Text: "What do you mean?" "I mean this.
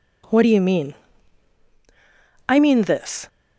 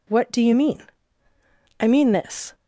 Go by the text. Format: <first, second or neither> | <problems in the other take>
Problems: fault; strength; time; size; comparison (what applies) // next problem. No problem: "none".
neither | none